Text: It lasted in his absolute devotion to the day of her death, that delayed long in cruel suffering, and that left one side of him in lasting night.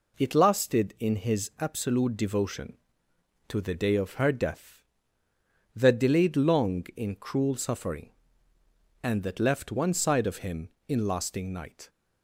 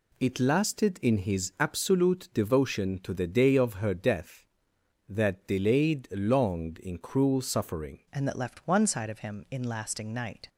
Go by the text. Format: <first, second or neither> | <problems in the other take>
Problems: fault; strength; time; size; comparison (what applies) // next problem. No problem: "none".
first | changes voice at "and"; from 8.1 s on; 2.3 s long